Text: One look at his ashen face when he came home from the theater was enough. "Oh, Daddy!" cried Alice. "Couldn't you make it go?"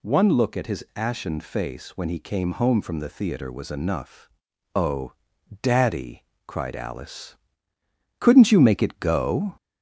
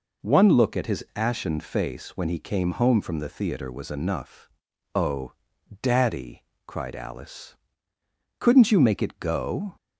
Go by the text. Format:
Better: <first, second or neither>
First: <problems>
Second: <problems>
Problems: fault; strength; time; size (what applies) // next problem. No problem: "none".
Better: second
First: gets louder; slight; throughout; 2.5 dB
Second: none